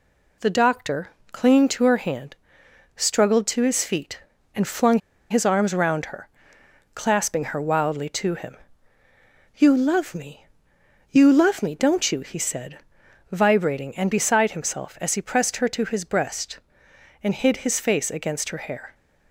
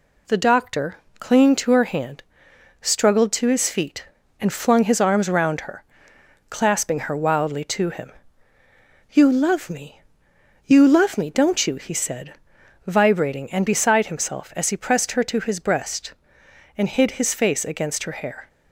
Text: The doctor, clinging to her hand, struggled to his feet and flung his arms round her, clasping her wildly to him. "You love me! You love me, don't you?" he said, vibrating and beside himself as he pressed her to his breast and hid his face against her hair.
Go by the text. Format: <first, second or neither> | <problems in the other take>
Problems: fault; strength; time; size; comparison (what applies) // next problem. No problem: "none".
second | pauses between "flung" and "his"; slight; at 4.9 s; 0.30 s long